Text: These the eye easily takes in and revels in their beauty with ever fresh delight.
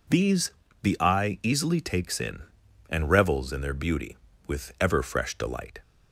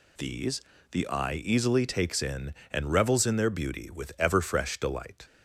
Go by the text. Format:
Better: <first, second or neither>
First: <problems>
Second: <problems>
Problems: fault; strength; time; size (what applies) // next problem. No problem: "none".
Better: neither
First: pauses between "These" and "the"; slight; at 0.5 s; 0.28 s long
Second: pauses between "These" and "the"; slight; at 0.6 s; 0.30 s long